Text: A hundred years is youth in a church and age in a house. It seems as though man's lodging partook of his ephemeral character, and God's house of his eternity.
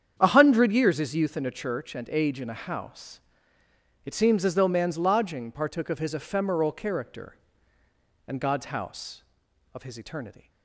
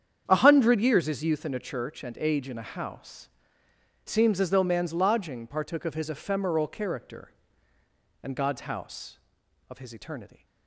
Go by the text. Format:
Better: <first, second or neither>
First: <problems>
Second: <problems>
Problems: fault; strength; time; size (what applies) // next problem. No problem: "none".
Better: first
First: starts louder than the rest; strong; until 1.1 s; 8.5 dB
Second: starts louder than the rest; strong; until 1.2 s; 8.5 dB // skips "It"; at 3.6 s